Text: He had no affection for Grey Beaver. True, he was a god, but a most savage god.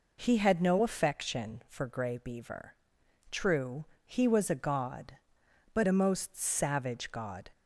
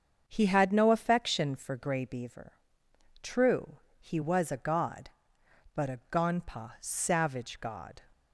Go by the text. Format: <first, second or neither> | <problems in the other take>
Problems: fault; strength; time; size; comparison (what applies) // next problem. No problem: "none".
first | starts louder than the rest; until 1.2 s; 6.5 dB // says "gonpa" for "most"; at 6.1 s